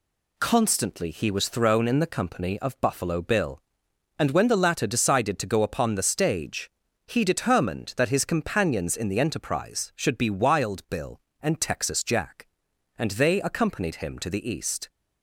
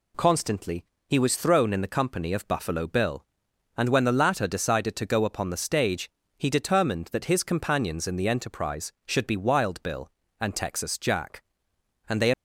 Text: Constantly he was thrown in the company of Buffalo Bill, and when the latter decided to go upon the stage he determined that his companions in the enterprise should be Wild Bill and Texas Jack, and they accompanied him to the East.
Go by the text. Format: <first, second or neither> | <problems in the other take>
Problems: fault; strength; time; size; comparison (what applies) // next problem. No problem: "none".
first | pauses between "Constantly" and "he"; slight; at 0.8 s; 0.22 s long // pauses between "stage" and "he"; slight; at 6.0 s; 0.28 s long; slight in the first // stops before "accompanied him to the East"; at 12.3 s